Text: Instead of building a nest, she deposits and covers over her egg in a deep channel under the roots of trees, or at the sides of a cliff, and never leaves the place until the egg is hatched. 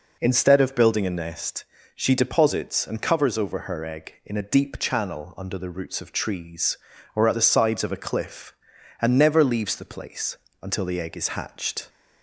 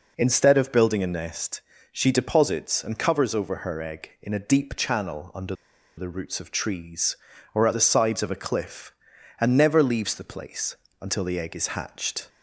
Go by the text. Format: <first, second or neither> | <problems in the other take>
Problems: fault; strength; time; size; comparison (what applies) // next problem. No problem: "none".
first | pauses between "under" and "the"; at 5.5 s; 0.42 s long // pauses between "place" and "until"; slight; at 10.7 s; 0.24 s long; slight in the first